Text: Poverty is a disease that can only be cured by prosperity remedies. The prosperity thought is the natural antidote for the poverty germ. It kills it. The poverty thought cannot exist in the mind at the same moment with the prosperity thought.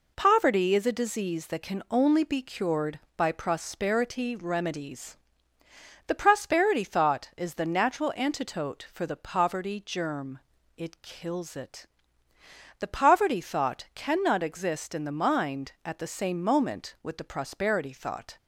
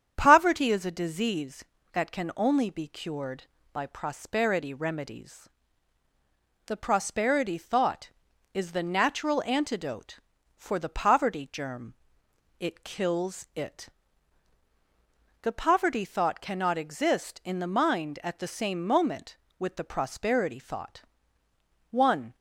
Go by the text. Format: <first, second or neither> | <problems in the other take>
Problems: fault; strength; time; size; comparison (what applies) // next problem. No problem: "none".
first | starts louder than the rest; strong; until 1.1 s; 8.5 dB // goes on to say "One"; slight; from 21.9 s on; 0.44 s long